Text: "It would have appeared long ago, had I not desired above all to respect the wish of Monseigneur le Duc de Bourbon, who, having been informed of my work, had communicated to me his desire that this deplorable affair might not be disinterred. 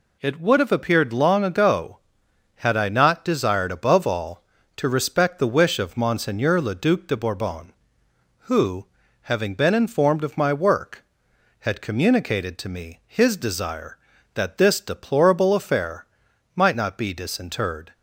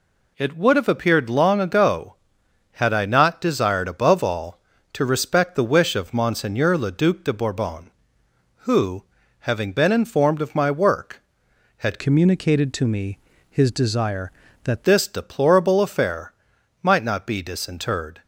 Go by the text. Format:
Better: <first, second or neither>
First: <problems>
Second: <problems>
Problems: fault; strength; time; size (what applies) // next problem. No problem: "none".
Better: first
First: pauses between "affair" and "might"; noticeable; at 16.0 s; 0.48 s long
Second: changes voice from "communicated" to "that"; from 11.9 to 14.8 s; 2.9 s long // pauses between "me" and "his"; slight; at 13.1 s; 0.32 s long // pauses between "affair" and "might"; noticeable; at 16.3 s; 0.48 s long